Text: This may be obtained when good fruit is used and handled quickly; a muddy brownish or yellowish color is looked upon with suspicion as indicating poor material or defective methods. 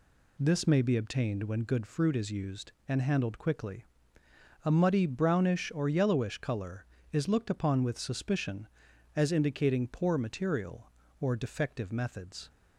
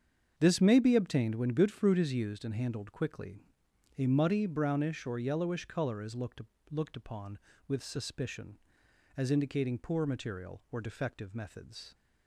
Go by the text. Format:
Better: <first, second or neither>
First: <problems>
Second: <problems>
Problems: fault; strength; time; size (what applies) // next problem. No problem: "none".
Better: first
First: none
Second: starts louder than the rest; strong; until 1.3 s; 7 dB // says "looked" twice; at 6.7 s